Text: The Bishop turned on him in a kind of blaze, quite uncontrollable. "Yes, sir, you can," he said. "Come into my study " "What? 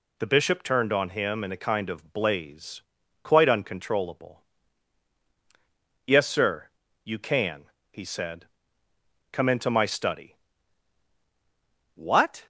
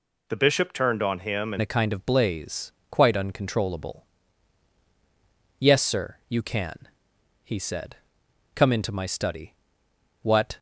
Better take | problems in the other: first | changes voice at "a"; from 1.6 s on; 8.9 s long

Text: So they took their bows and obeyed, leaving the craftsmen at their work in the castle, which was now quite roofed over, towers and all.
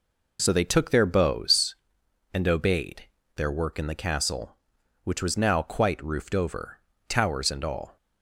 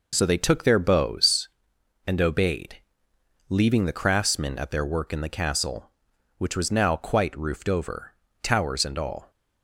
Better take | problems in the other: second | skips "leaving the craftsmen at"; at 3.1 s

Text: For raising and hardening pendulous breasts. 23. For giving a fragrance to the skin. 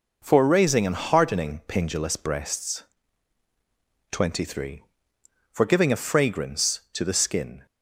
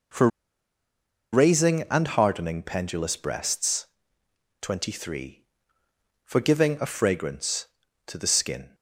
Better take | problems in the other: first | pauses between "For" and "raising"; at 0.2 s; 1.0 s long

